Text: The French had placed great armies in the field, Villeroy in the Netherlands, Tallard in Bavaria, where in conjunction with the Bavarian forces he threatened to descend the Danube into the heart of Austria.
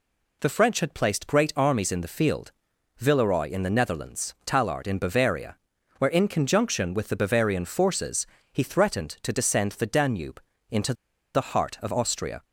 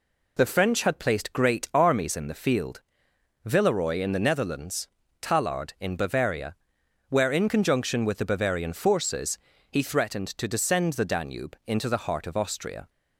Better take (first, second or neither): second